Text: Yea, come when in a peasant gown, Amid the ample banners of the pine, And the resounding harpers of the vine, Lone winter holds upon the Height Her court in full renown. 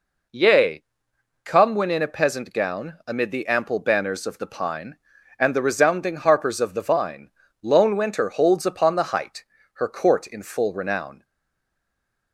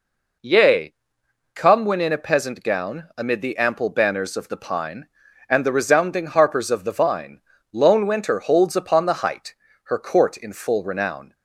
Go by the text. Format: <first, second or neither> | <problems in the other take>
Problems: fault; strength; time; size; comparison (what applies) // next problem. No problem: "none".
second | pauses between "Height" and "Her"; slight; at 9.4 s; 0.30 s long; slight in the second // stays silent after the last word; from 11.2 s on; 1.1 s long